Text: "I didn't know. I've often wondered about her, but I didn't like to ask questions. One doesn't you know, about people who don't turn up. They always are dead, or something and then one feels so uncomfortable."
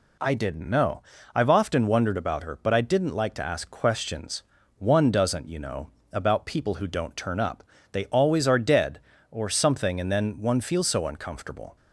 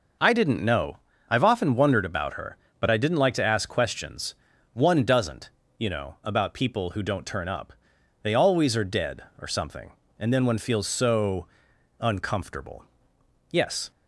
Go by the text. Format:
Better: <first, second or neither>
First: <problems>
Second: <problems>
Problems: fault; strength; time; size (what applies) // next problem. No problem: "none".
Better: first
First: none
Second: pauses between "doesn't" and "you"; slight; at 5.5 s; 0.28 s long // pauses between "so" and "uncomfortable"; noticeable; at 11.4 s; 0.54 s long // goes on to say "Yes"; slight; from 13.5 s on; 0.38 s long